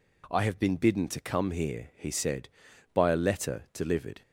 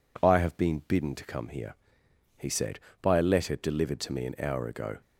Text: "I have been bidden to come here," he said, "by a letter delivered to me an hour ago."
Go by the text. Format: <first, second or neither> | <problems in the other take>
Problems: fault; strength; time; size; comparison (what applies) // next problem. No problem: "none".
second | stops before "to me an hour ago"; at 4.2 s